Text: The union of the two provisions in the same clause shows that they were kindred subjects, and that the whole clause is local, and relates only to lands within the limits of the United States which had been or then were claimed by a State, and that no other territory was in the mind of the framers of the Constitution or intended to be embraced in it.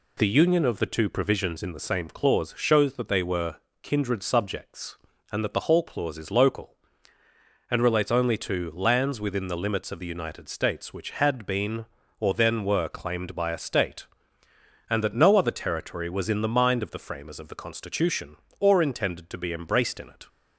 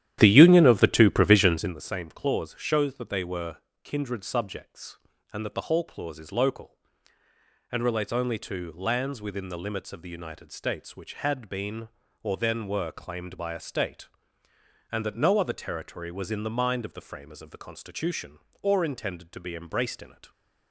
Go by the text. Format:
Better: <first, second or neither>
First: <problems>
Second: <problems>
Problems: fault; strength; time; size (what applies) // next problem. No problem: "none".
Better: first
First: pauses between "were" and "kindred"; slight; at 3.5 s; 0.28 s long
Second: starts louder than the rest; strong; until 1.8 s; 11.5 dB // pauses between "were" and "kindred"; slight; at 3.5 s; 0.28 s long